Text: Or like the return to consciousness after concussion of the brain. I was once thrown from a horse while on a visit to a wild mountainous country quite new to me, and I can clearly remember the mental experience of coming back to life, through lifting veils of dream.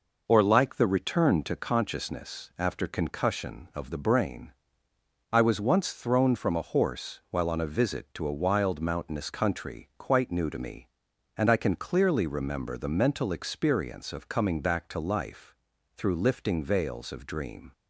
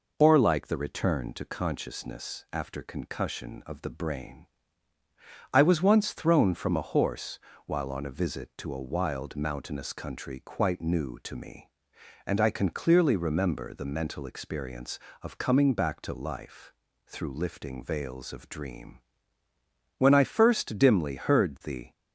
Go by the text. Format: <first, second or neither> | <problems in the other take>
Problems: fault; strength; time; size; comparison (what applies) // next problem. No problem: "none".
first | pauses between "horse" and "while"; slight; at 7.3 s; 0.28 s long // goes on to say "When I first dimly heard the"; strong; from 19.9 s on; 1.9 s long